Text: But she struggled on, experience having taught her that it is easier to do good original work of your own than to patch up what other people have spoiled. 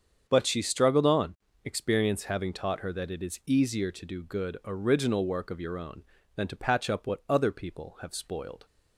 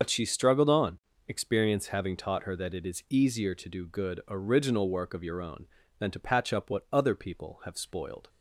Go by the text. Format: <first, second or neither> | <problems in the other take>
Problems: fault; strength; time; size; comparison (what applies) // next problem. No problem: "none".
first | loses the start of "But"; at 0.0 s; 85 ms // starts louder than the rest; until 1.2 s; 6.5 dB; strong in the first